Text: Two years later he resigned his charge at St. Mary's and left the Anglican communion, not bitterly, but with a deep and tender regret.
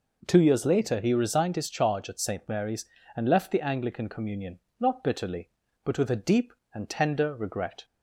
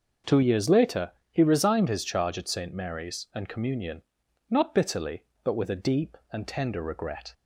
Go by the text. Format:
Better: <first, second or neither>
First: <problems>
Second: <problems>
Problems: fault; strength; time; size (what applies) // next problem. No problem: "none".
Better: first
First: none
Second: starts louder than the rest; noticeable; until 1.4 s; 6 dB // pauses between "later" and "he"; slight; at 1.1 s; 0.20 s long // skips "left the Anglican"; at 3.4 s